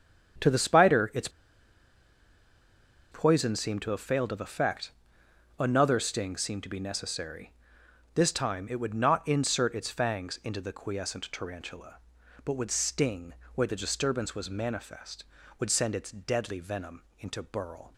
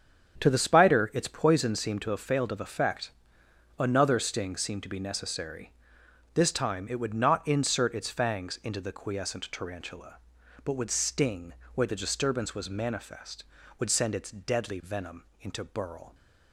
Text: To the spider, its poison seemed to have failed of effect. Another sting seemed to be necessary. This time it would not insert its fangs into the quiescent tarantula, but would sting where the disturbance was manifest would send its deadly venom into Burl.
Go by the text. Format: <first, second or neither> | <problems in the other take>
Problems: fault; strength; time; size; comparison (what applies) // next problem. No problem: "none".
second | starts louder than the rest; strong; until 3.3 s; 8.5 dB; strong in the second // pauses between "its" and "poison"; strong; at 1.2 s; 1.8 s long // pauses between "sting" and "where"; slight; at 13.3 s; 0.18 s long; slight in the second // pauses between "venom" and "into"; slight; at 17.0 s; 0.16 s long; slight in the second